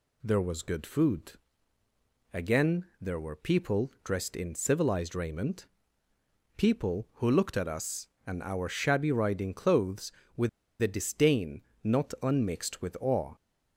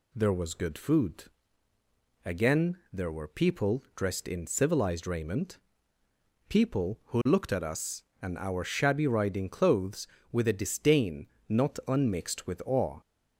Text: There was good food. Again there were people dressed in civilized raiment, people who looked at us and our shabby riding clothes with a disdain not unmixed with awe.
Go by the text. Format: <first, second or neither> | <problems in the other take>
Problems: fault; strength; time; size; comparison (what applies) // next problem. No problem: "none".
second | pauses between "Again" and "there"; slight; at 2.8 s; 0.16 s long; slight in the second // pauses between "with" and "a"; slight; at 10.4 s; 0.32 s long // pauses between "disdain" and "not"; slight; at 11.6 s; 0.22 s long; slight in the second